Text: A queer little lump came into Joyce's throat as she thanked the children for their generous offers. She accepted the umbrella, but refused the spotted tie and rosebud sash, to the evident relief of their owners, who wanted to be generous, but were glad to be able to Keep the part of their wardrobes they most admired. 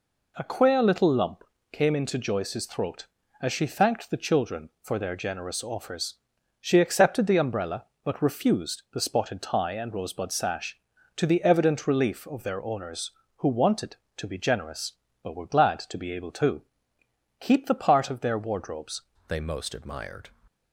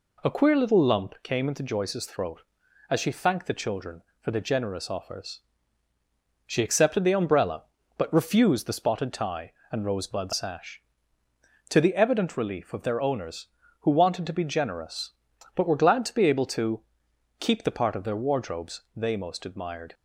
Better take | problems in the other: second | pauses between "lump" and "came"; slight; at 1.4 s; 0.26 s long // pauses between "to" and "Keep"; noticeable; at 16.6 s; 0.78 s long; noticeable in the second // changes voice at "they"; from 19.2 s on; 1.0 s long

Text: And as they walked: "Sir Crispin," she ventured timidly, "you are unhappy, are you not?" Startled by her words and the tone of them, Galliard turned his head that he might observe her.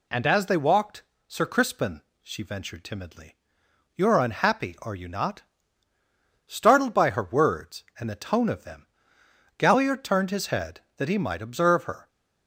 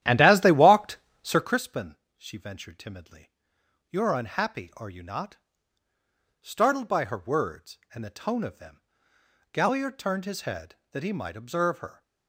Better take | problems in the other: first | starts louder than the rest; strong; until 1.6 s; 12 dB

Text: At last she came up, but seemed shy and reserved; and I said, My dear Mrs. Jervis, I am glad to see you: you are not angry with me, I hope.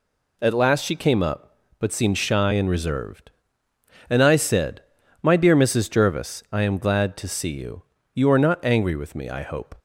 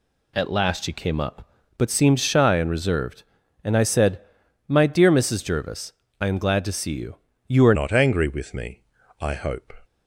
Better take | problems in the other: first | changes voice at "not"; from 7.7 s on; 2.0 s long

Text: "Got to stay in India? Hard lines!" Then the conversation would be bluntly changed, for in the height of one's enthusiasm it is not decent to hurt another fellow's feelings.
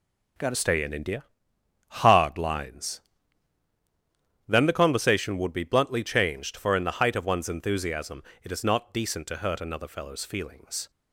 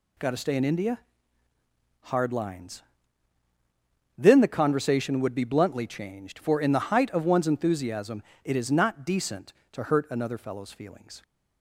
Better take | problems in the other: second | starts louder than the rest; until 2.1 s; 7 dB // changes voice at "stay"; from 0.5 s on; 10.3 s long // pauses between "enthusiasm" and "it"; slight; at 8.2 s; 0.20 s long; slight in the second

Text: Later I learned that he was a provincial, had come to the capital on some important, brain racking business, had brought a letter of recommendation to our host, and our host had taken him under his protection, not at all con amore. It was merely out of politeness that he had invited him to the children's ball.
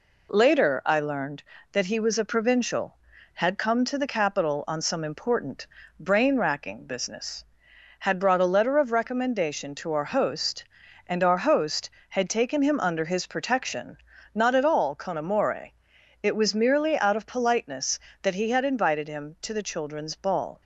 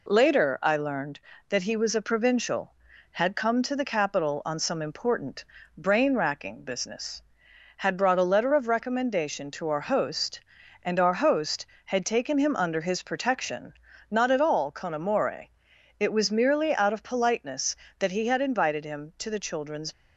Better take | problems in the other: first | stops before "ball"; at 19.9 s

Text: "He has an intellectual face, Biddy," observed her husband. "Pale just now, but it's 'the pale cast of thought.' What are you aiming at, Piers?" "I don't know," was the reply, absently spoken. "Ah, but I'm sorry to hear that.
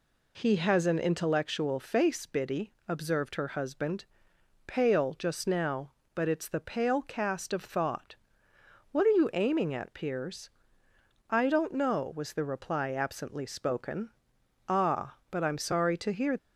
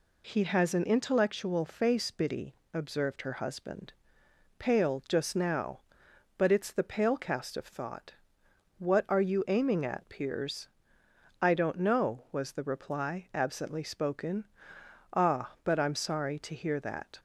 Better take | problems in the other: second | stops before "that"; at 16.3 s

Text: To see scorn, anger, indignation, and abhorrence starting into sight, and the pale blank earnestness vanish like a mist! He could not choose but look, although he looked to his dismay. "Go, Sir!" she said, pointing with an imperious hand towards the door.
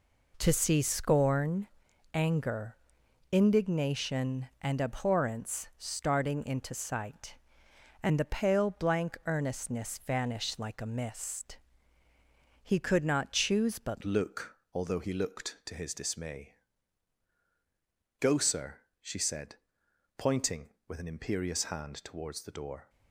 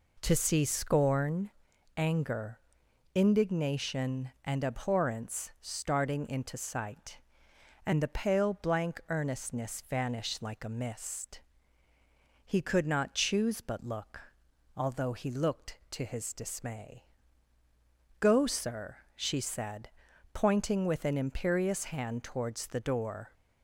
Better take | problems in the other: second | changes voice at "look"; from 14.0 s on; 8.8 s long

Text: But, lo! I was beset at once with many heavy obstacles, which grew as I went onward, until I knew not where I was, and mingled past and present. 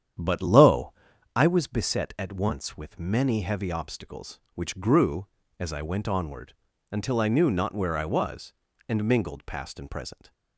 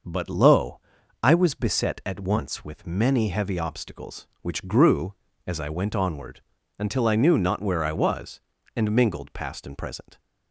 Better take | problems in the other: second | starts louder than the rest; strong; until 1.3 s; 9 dB

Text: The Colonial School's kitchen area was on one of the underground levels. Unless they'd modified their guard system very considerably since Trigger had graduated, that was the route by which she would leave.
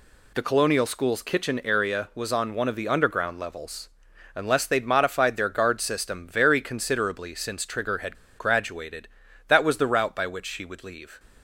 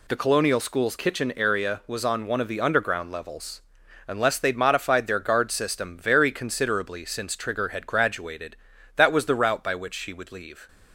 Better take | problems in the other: second | pauses between "had" and "graduated"; slight; at 8.1 s; 0.23 s long

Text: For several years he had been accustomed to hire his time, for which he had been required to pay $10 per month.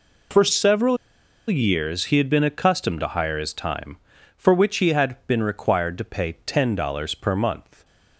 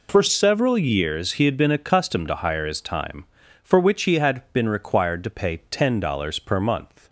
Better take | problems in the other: second | pauses between "several" and "years"; noticeable; at 0.9 s; 0.51 s long

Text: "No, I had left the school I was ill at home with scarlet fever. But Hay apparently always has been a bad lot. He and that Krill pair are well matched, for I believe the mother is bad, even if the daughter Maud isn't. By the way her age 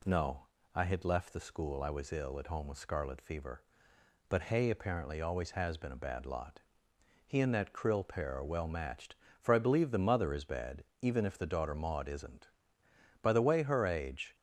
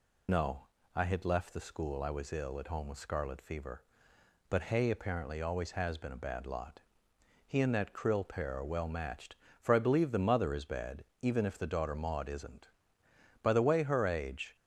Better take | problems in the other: first | loses the start of "No"; at 0.2 s; 65 ms

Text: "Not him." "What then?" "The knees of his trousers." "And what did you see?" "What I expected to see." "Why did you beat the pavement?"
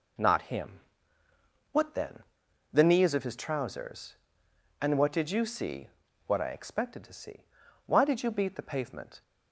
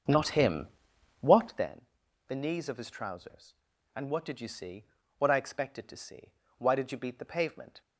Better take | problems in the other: first | starts louder than the rest; until 1.7 s; 7 dB

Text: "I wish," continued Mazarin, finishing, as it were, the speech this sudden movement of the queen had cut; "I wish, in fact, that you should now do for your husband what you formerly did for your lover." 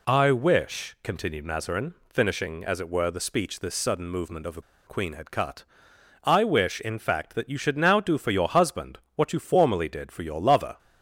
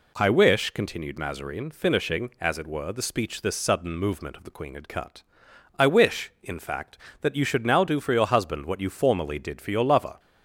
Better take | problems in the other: second | pauses between "the" and "queen"; slight; at 4.6 s; 0.25 s long // pauses between "husband" and "what"; slight; at 8.9 s; 0.16 s long

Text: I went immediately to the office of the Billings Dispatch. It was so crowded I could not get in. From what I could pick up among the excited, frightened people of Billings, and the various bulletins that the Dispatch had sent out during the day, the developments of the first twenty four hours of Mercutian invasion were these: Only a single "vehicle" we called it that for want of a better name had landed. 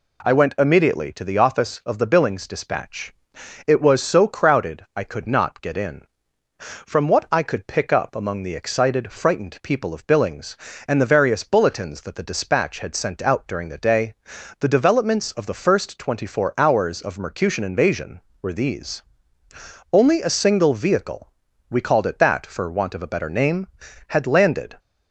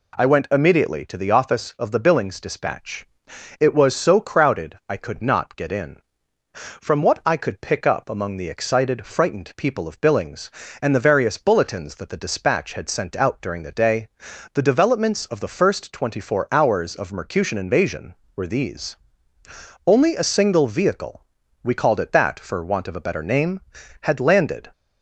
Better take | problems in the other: neither | pauses between "vehicle" and "we"; the same in both

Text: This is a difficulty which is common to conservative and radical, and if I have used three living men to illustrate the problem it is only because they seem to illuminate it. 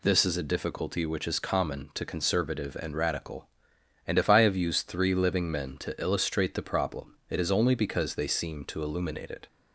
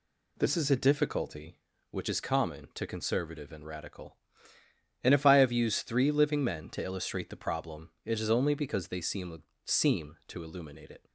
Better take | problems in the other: first | says "seem" twice; at 9.6 s

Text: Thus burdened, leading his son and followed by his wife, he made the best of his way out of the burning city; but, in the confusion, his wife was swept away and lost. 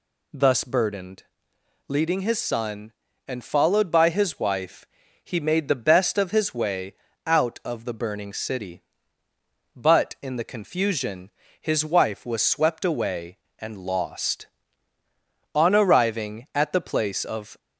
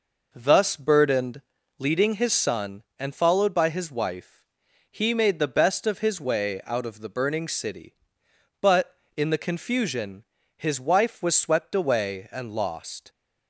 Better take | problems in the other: second | pauses between "way" and "out"; slight; at 6.9 s; 0.30 s long // goes on to say "On arriving at the place of"; strong; from 15.5 s on; 2.0 s long

